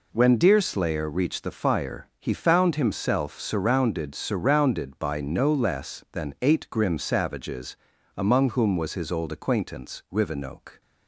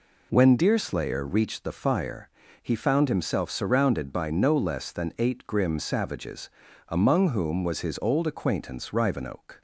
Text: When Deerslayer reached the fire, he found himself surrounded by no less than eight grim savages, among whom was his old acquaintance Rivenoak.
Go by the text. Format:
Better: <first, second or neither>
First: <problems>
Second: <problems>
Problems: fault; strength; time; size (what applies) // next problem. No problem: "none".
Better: second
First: says "surrounded" twice; at 4.1 s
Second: none